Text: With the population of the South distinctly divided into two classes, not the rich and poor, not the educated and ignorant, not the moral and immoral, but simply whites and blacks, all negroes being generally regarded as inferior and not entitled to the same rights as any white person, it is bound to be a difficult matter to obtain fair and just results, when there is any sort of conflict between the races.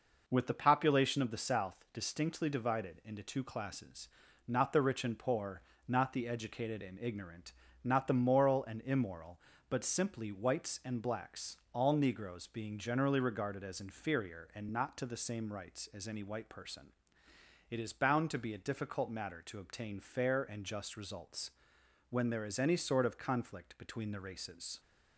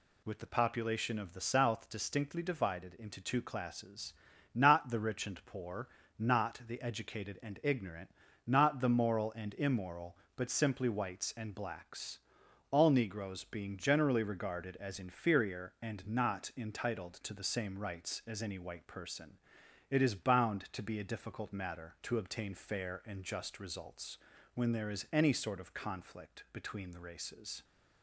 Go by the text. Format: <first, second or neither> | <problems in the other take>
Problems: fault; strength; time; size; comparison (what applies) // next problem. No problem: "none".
second | skips "entitled"; at 14.9 s